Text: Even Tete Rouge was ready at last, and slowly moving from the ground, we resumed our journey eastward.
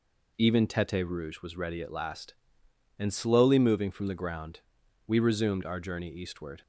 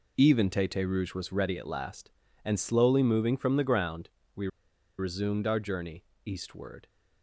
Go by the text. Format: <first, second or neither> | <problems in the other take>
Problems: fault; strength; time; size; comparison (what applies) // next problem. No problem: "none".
first | pauses between "we" and "resumed"; noticeable; at 4.4 s; 0.51 s long // pauses between "journey" and "eastward"; slight; at 6.0 s; 0.22 s long